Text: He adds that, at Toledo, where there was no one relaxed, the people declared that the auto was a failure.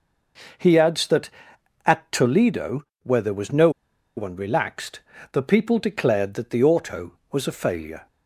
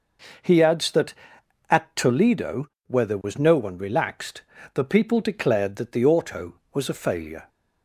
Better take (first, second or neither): second